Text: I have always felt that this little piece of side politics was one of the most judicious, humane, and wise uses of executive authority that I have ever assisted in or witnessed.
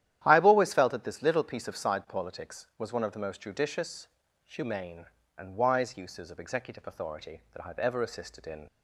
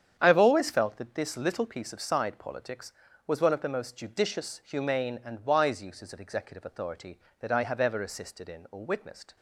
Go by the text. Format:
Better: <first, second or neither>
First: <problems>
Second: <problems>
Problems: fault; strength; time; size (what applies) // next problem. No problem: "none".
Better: second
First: starts louder than the rest; strong; until 1.2 s; 11.5 dB // stops before "or witnessed"; at 8.6 s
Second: starts louder than the rest; strong; until 1.2 s; 8.5 dB